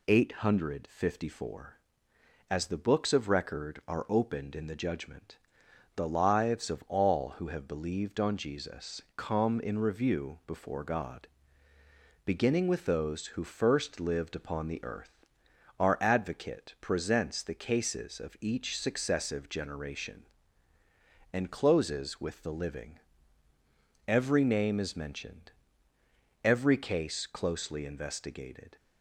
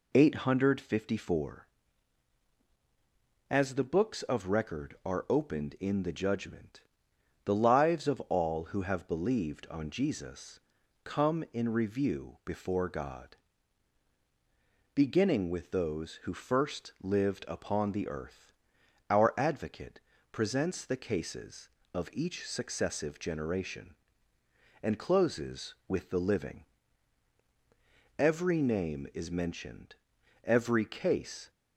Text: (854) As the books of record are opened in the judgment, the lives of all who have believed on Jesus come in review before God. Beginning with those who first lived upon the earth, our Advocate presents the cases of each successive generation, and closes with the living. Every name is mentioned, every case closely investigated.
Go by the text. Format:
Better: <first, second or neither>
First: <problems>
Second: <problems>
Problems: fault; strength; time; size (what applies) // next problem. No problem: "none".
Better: first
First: pauses between "Jesus" and "come"; slight; at 8.9 s; 0.16 s long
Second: pauses between "Jesus" and "come"; at 10.5 s; 0.44 s long // pauses between "Advocate" and "presents"; slight; at 20.0 s; 0.28 s long // stops before "closely investigated"; at 31.4 s